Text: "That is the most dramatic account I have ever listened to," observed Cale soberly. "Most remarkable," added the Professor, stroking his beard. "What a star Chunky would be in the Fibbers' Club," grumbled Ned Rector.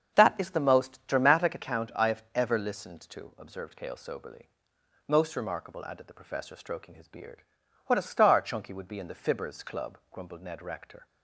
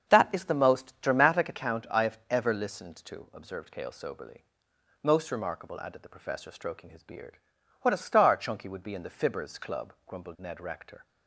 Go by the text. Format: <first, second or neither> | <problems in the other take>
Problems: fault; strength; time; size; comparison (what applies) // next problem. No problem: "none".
neither | starts louder than the rest; strong; the same in both